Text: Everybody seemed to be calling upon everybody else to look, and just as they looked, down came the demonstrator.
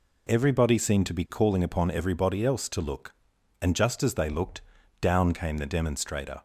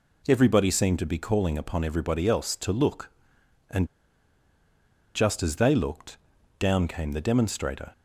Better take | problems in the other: first | pauses between "and" and "just"; strong; at 3.8 s; 1.3 s long

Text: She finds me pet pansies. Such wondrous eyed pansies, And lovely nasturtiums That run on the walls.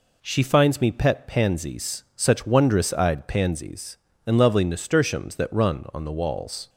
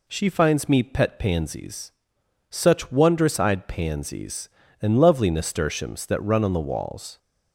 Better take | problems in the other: neither | none

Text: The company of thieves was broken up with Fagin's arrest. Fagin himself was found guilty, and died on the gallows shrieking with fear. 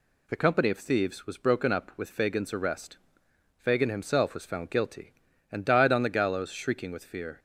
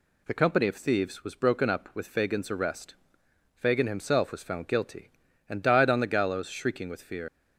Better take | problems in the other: first | leaves "fear" unfinished; at 7.2 s; 80 ms

